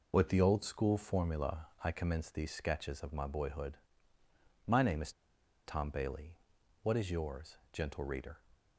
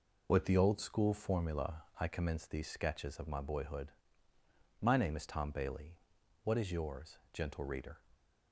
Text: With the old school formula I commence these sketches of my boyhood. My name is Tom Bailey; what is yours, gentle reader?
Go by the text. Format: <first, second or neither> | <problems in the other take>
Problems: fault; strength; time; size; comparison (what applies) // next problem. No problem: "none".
second | pauses between "formula" and "I"; slight; at 1.6 s; 0.16 s long; slight in the second // pauses between "is" and "Tom"; noticeable; at 5.1 s; 0.55 s long